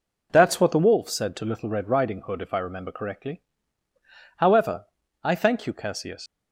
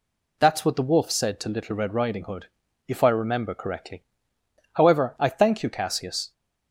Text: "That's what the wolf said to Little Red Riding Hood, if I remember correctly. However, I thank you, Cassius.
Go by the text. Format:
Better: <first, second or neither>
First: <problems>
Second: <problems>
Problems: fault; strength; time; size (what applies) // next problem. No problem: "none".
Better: second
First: leaves "Cassius" unfinished; at 6.2 s; 95 ms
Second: none